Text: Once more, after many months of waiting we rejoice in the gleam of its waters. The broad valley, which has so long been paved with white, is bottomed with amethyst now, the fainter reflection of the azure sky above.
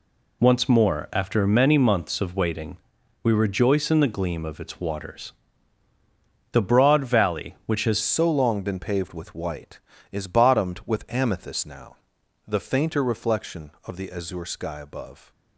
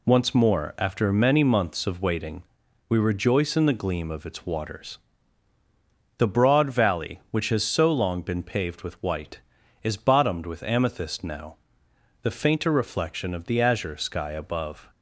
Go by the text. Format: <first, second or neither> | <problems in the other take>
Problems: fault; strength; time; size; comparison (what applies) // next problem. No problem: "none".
second | pauses between "waiting" and "we"; noticeable; at 2.7 s; 0.46 s long; noticeable in the second // changes voice at "so"; from 8.0 s on; 7.3 s long